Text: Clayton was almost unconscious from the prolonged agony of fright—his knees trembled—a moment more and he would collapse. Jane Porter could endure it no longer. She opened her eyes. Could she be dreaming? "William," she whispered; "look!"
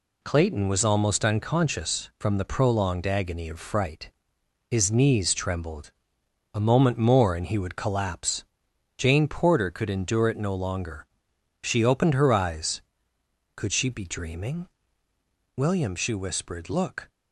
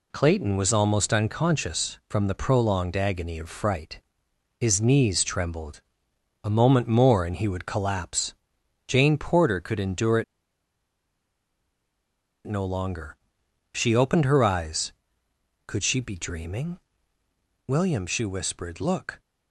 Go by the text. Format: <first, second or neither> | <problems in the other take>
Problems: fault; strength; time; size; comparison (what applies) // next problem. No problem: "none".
first | pauses between "it" and "no"; strong; at 10.2 s; 2.2 s long